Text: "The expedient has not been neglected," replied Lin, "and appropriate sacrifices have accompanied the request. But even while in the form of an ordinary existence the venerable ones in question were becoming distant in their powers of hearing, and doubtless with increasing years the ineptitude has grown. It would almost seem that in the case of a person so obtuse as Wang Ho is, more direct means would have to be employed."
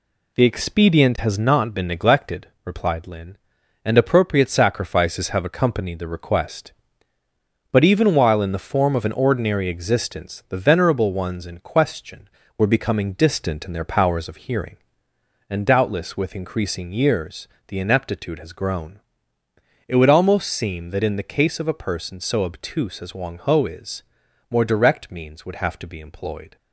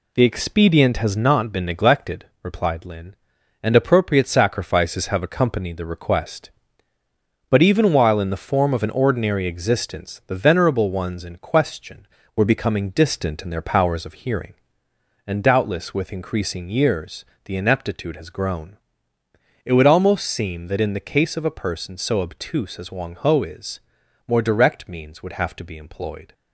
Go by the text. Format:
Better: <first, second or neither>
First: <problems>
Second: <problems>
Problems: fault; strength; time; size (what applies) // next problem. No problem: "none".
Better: neither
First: pauses between "years" and "the"; slight; at 17.4 s; 0.22 s long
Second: pauses between "years" and "the"; slight; at 17.2 s; 0.22 s long